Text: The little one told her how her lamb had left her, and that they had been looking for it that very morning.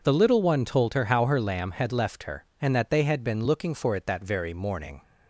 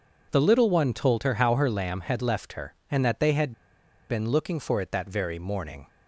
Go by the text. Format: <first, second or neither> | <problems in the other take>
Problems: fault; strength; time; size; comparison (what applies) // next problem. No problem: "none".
first | pauses between "had" and "been"; noticeable; at 3.5 s; 0.57 s long